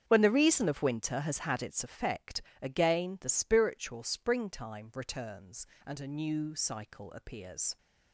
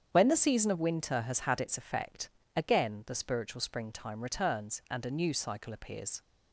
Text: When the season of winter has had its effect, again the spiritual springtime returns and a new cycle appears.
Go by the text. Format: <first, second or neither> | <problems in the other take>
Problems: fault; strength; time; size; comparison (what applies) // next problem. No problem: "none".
second | starts louder than the rest; strong; until 1.0 s; 8 dB; strong in the second // says "reason" for "season"; at 0.3 s